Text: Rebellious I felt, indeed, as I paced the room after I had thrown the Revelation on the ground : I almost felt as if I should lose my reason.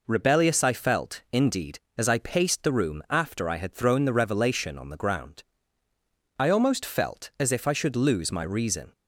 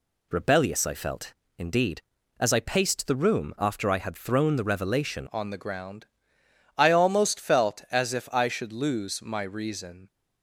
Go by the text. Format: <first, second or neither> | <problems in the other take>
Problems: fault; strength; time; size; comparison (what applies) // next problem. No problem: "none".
first | changes voice at "on"; from 5.3 s on; 4.7 s long